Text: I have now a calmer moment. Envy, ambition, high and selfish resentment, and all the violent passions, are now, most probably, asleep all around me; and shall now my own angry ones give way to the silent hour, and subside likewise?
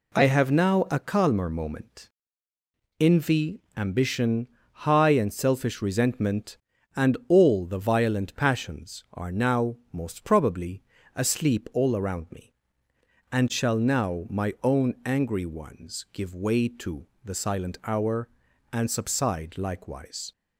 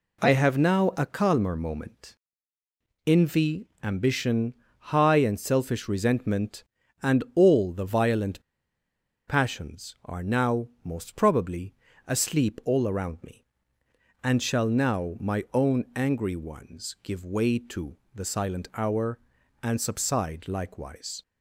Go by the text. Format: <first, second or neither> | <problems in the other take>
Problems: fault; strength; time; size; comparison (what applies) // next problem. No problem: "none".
first | pauses between "violent" and "passions"; noticeable; at 8.4 s; 0.85 s long // pauses between "to" and "the"; slight; at 17.9 s; 0.16 s long; slight in the first